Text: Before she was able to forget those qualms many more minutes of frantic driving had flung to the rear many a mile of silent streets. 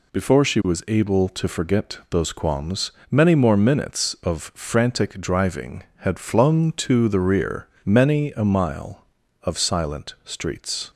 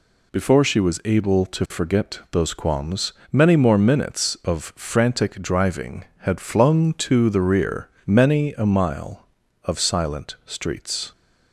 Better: neither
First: pauses between "qualms" and "many"; slight; at 2.8 s; 0.20 s long // pauses between "rear" and "many"; slight; at 7.6 s; 0.16 s long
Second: pauses between "qualms" and "many"; slight; at 3.1 s; 0.20 s long // pauses between "rear" and "many"; slight; at 7.8 s; 0.16 s long

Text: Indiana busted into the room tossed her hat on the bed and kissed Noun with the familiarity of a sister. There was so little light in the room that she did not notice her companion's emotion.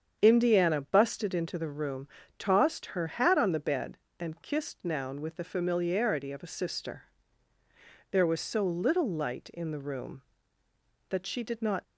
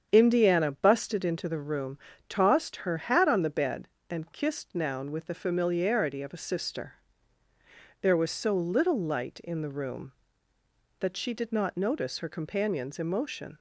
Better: second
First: starts louder than the rest; strong; until 1.2 s; 7.5 dB // pauses between "room" and "tossed"; slight; at 2.0 s; 0.30 s long // stops before "notice her companion's emotion"; at 11.8 s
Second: starts louder than the rest; strong; until 1.1 s; 7.5 dB // pauses between "room" and "tossed"; slight; at 1.9 s; 0.30 s long

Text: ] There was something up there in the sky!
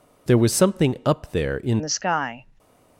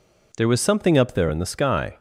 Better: second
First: changes voice at "the"; from 1.8 s on; 0.6 s long // stays silent after the last word; slight; from 2.4 s on; 0.5 s long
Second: none

